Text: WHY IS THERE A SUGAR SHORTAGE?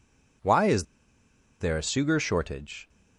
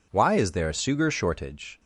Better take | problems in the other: second | pauses between "IS" and "THERE"; noticeable; at 0.8 s; 0.75 s long

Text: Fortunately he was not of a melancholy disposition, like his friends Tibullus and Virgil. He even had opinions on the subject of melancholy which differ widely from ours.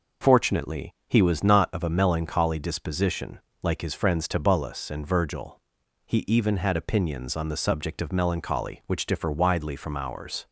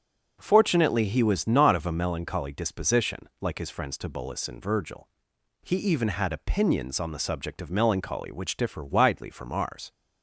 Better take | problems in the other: neither | none

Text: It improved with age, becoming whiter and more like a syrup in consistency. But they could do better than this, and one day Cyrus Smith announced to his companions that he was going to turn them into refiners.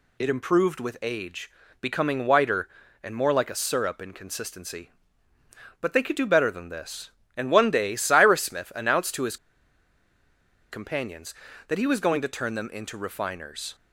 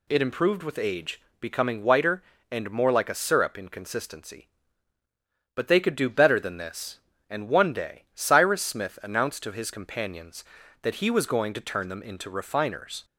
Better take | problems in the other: second | pauses between "his" and "companions"; strong; at 9.3 s; 1.3 s long

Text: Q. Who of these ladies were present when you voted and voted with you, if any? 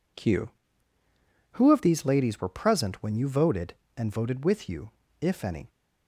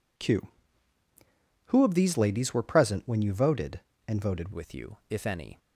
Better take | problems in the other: first | changes voice at "with"; from 4.5 s on; 1.0 s long

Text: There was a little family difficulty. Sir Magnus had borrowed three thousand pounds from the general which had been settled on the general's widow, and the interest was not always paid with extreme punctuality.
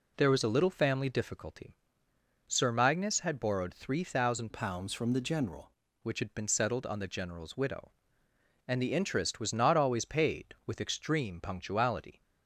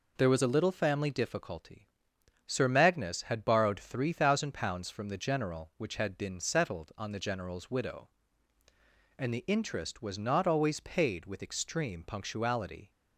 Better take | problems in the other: second | changes voice from "pounds" to "general"; from 4.5 to 5.7 s; 1.2 s long

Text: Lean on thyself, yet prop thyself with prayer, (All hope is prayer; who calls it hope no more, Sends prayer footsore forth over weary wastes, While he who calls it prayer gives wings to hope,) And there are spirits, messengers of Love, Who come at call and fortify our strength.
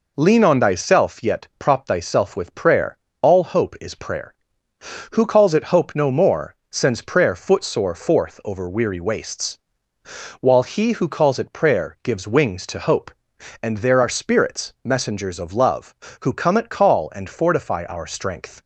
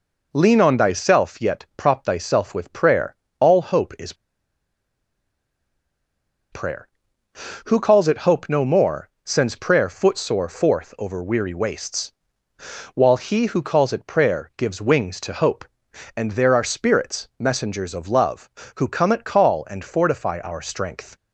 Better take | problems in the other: first | pauses between "is" and "prayer"; strong; at 4.1 s; 2.3 s long

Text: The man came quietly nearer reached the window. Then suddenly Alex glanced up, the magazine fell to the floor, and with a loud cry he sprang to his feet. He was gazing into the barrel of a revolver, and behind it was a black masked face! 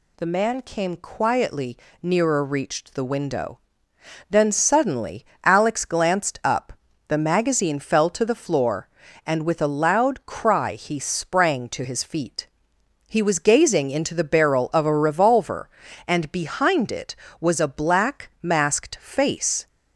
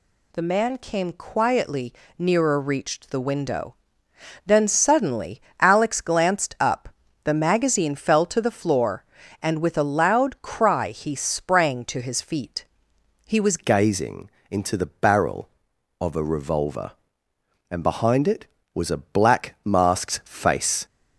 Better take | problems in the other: first | pauses between "quietly" and "nearer"; slight; at 1.9 s; 0.26 s long; slight in the first // pauses between "suddenly" and "Alex"; slight; at 5.4 s; 0.20 s long; slight in the first // changes voice at "gazing"; from 13.5 s on; 7.3 s long // pauses between "gazing" and "into"; slight; at 14.2 s; 0.22 s long

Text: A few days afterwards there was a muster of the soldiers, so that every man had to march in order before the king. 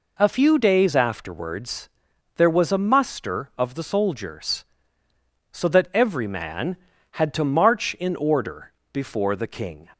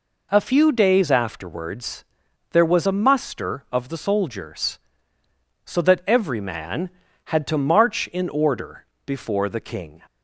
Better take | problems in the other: neither | pauses between "afterwards" and "there"; noticeable; the same in both // pauses between "order" and "before"; slight; the same in both

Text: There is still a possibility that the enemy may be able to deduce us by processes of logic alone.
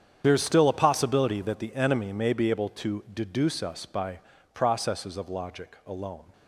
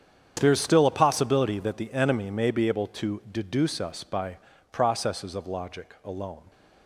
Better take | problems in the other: second | loses the start of "There"; at 0.2 s; 55 ms // starts louder than the rest; strong; until 1.2 s; 8.5 dB; strong in the second // pauses between "by" and "processes"; slight; at 4.1 s; 0.34 s long; slight in the second

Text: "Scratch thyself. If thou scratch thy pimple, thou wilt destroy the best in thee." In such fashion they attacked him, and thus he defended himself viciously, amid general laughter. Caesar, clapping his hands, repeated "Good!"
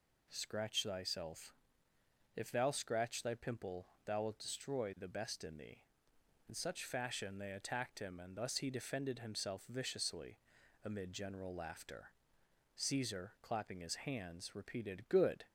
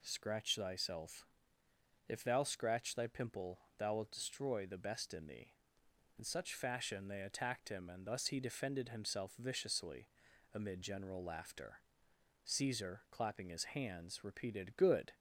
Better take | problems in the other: neither | none

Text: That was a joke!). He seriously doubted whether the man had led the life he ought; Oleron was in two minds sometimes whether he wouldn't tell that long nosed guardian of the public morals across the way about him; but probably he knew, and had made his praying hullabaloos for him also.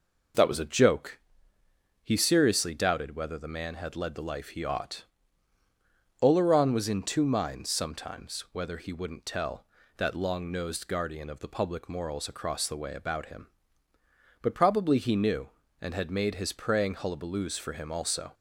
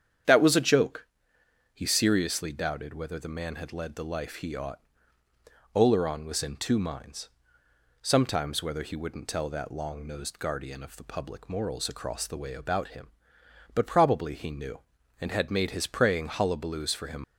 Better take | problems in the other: first | starts louder than the rest; strong; until 1.9 s; 8.5 dB // pauses between "minds" and "sometimes"; noticeable; at 7.2 s; 0.74 s long // stops before "also"; at 17.2 s

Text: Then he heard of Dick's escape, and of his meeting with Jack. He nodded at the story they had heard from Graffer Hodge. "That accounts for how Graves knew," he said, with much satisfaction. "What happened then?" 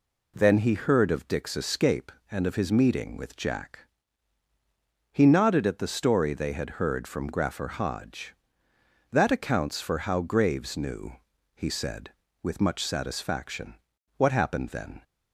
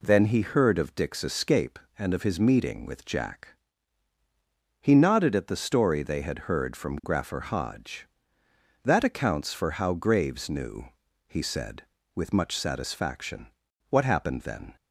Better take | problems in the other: neither | none

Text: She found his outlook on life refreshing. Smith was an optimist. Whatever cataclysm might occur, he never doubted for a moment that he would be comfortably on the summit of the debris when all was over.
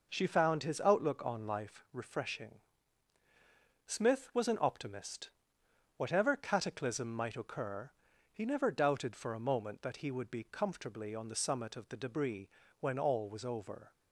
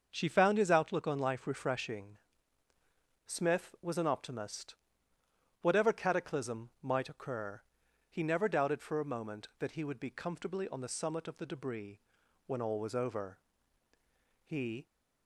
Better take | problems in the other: first | starts louder than the rest; until 1.1 s; 6.5 dB // pauses between "debris" and "when"; at 12.0 s; 0.44 s long; slight in the first // goes on to say "He"; slight; from 14.4 s on; 0.42 s long

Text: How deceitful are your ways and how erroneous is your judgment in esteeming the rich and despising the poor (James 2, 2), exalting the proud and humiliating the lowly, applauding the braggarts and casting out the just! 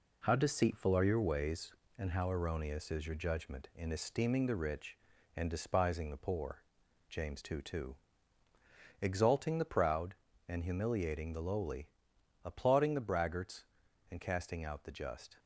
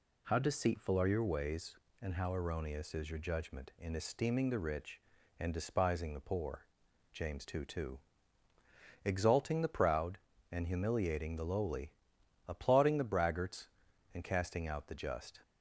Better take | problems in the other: second | gets quieter; noticeable; throughout; 5 dB

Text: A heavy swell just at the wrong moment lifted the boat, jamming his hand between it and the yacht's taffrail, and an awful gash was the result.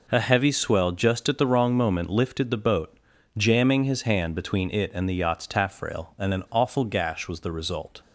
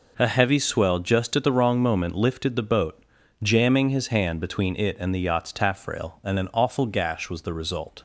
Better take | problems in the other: neither | none

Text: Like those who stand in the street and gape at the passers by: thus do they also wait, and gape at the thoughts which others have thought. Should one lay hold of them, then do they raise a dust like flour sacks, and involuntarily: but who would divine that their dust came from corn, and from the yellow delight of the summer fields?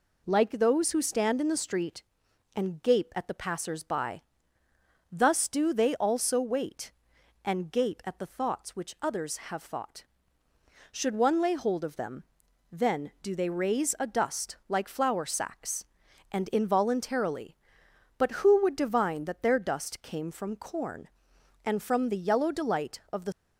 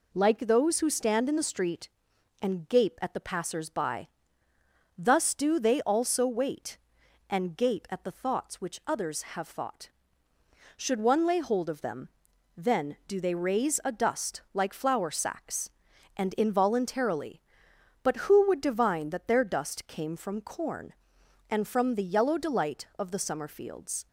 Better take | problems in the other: second | stops before "summer fields"; at 23.3 s

